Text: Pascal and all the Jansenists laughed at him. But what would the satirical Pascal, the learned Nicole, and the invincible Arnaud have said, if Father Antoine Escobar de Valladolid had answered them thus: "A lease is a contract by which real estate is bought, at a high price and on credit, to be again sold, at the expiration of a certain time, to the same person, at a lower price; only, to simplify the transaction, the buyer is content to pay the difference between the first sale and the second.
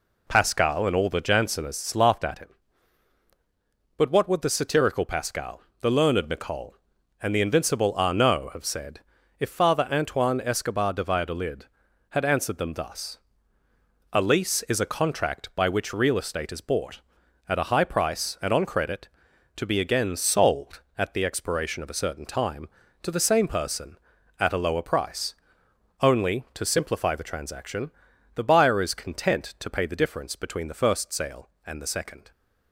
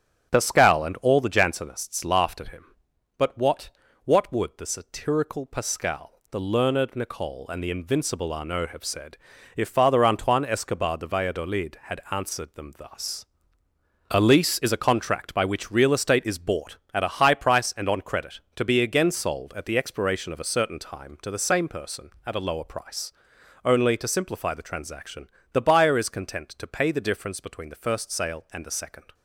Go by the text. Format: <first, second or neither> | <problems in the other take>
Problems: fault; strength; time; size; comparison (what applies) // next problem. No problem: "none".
first | starts louder than the rest; strong; until 1.3 s; 10 dB // says "what" twice; at 4.0 s